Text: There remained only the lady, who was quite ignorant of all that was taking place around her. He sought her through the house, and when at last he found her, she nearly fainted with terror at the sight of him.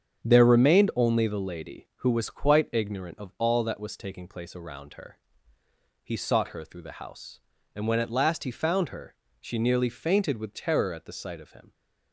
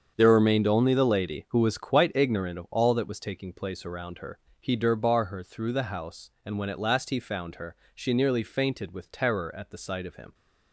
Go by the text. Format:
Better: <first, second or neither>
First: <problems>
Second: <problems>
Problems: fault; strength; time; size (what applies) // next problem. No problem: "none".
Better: first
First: starts louder than the rest; strong; until 1.2 s; 7.5 dB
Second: starts louder than the rest; strong; until 1.1 s; 7.5 dB // says "durbar" for "sought"; at 4.7 s